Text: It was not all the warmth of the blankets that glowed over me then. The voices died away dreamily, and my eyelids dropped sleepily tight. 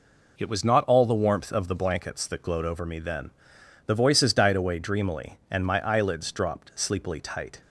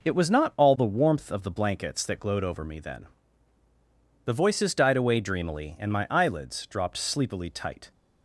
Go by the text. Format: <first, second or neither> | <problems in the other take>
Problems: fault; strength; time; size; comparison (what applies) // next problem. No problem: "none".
neither | none